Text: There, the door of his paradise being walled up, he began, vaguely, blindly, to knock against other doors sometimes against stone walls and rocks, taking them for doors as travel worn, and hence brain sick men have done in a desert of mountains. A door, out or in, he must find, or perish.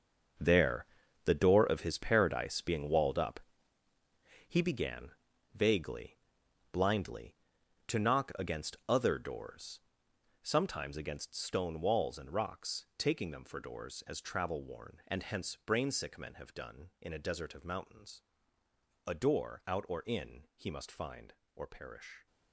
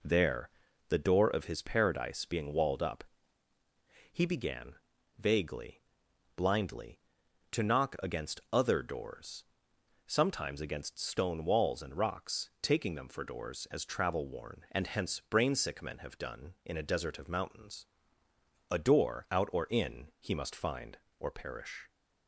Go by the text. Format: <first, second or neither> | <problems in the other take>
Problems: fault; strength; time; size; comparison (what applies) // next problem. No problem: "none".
second | gets quieter; strong; throughout; 12.5 dB // pauses between "doors" and "sometimes"; noticeable; at 9.7 s; 0.66 s long; noticeable in the second